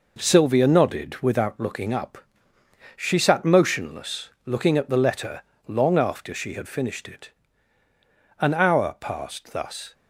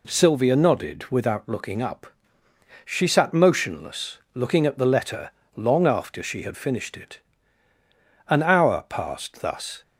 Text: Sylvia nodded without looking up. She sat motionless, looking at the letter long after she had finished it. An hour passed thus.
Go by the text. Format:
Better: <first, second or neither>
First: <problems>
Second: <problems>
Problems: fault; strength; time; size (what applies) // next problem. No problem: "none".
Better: second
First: gets quieter; throughout; 6.5 dB // pauses between "letter" and "long"; slight; at 5.4 s; 0.24 s long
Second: pauses between "letter" and "long"; slight; at 5.3 s; 0.24 s long